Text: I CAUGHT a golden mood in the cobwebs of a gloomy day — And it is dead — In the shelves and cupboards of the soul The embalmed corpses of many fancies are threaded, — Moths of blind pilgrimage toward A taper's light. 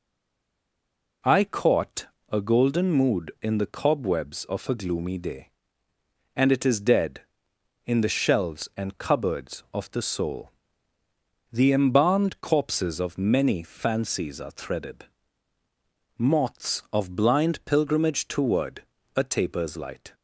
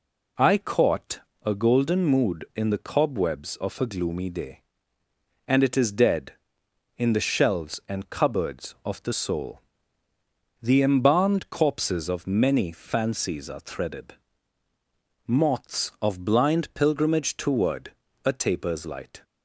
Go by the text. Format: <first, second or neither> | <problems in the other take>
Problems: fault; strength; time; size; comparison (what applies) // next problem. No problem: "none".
second | stays silent before the first word; noticeable; until 1.2 s; 1.2 s long // pauses between "CAUGHT" and "a"; slight; at 2.0 s; 0.22 s long; slight in the second // pauses between "soul" and "The"; noticeable; at 10.5 s; 0.98 s long; noticeable in the second // pauses between "toward" and "A"; slight; at 18.8 s; 0.30 s long; slight in the second